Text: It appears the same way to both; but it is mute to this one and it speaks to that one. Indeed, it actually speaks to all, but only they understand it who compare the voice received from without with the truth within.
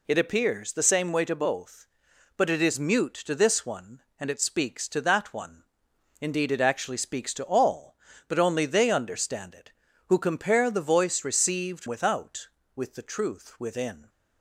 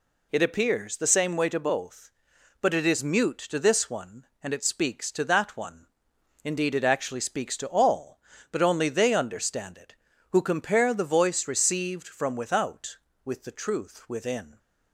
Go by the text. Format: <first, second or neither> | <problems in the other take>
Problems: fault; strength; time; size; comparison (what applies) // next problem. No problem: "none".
second | skips "from"; at 11.8 s